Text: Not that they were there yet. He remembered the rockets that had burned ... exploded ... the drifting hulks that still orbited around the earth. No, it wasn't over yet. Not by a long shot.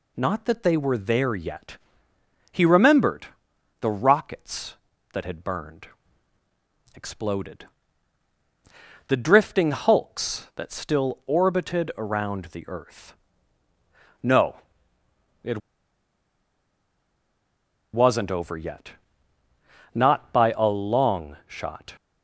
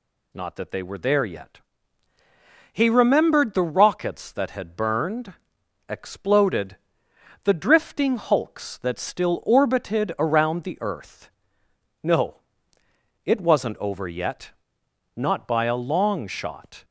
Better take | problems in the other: second | pauses between "remembered" and "the"; noticeable; at 3.2 s; 0.54 s long // pauses between "it" and "wasn't"; strong; at 15.5 s; 2.3 s long

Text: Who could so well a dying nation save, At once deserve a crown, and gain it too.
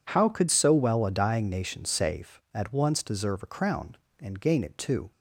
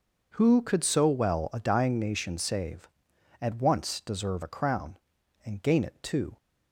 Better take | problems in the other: second | says "How" for "Who"; at 0.0 s

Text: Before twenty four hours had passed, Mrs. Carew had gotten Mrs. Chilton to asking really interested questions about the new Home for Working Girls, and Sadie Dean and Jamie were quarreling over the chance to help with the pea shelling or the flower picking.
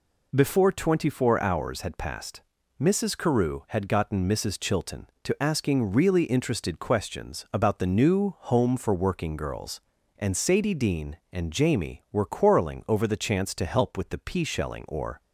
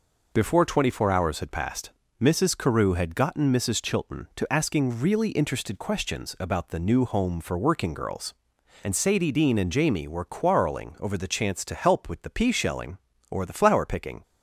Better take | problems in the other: second | stops before "the flower picking"; at 15.2 s

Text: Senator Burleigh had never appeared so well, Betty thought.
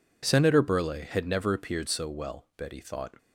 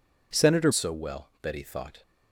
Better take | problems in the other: first | skips "Burleigh had never appeared"; at 0.7 s

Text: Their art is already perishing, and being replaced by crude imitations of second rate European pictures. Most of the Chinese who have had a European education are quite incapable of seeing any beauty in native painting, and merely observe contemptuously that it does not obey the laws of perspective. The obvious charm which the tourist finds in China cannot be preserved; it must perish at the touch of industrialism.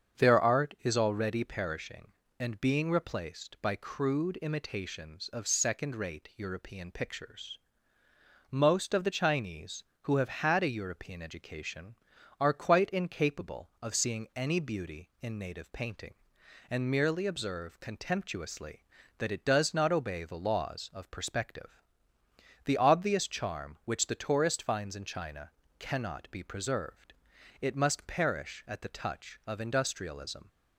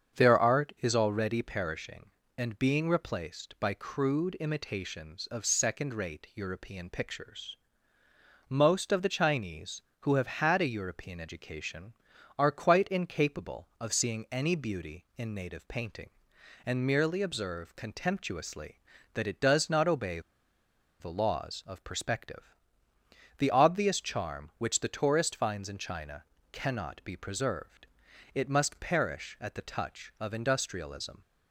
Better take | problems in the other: first | starts louder than the rest; strong; until 1.2 s; 7 dB; strong in the first // pauses between "obey" and "the"; noticeable; at 20.1 s; 0.80 s long // pauses between "China" and "cannot"; slight; at 26.2 s; 0.26 s long; slight in the first

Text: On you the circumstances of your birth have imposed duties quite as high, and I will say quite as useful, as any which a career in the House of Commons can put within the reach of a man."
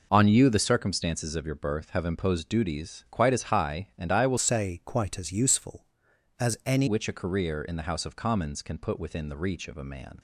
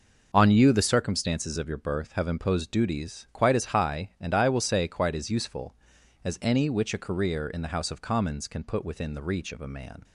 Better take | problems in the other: second | changes voice from "say" to "any"; from 4.3 to 6.8 s; 2.5 s long

